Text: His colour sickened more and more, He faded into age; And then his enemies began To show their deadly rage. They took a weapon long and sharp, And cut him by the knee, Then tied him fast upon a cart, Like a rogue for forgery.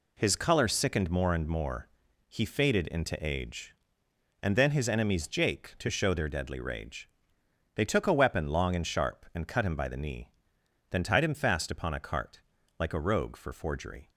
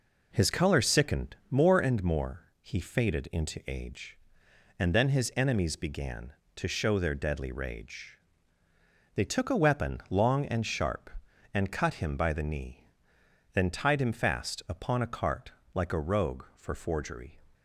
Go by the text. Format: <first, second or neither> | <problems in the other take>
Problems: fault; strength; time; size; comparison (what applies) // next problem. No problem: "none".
second | says "jake" for "began"; at 5.2 s